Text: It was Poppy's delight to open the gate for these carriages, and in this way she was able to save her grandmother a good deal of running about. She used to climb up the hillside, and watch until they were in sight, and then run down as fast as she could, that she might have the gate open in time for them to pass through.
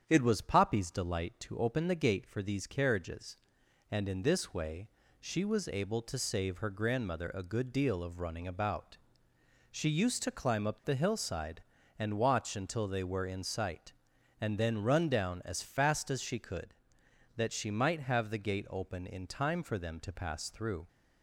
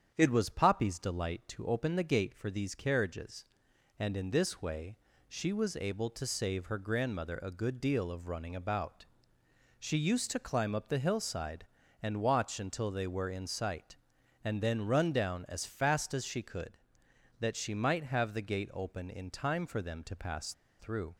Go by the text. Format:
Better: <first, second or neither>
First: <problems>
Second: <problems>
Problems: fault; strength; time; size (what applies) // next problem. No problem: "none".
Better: first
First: starts louder than the rest; strong; until 1.0 s; 8.5 dB // pauses between "way" and "she"; slight; at 4.8 s; 0.30 s long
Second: starts louder than the rest; strong; until 1.1 s; 8.5 dB // pauses between "way" and "she"; slight; at 4.9 s; 0.30 s long // pauses between "pass" and "through"; slight; at 20.5 s; 0.26 s long